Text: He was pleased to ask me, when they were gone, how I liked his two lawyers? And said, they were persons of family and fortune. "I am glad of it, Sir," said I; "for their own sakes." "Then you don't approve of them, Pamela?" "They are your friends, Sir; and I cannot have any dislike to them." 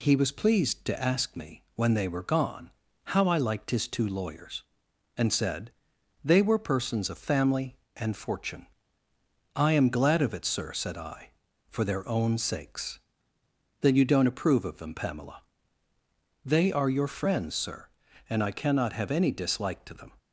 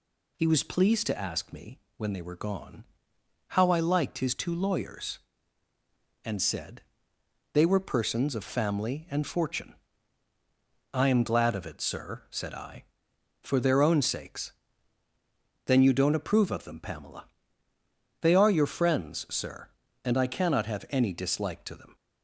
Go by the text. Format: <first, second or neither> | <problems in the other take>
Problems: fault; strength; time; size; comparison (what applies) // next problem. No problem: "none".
neither | none